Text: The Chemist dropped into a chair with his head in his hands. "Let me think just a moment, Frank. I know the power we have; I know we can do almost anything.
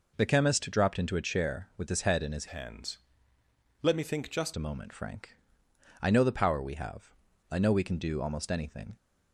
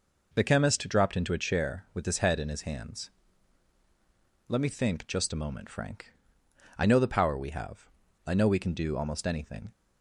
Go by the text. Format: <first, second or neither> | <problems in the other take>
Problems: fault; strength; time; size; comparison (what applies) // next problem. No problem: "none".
second | changes voice from "hands" to "just"; from 2.4 to 4.5 s; 2.1 s long